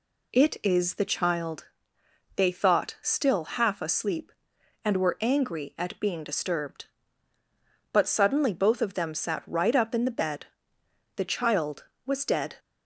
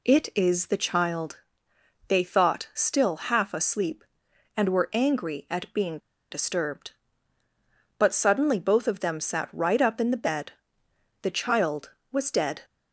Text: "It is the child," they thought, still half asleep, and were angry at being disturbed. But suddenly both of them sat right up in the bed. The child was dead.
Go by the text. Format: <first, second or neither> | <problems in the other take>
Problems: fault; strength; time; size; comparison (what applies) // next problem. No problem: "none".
first | pauses between "being" and "disturbed"; slight; at 5.9 s; 0.32 s long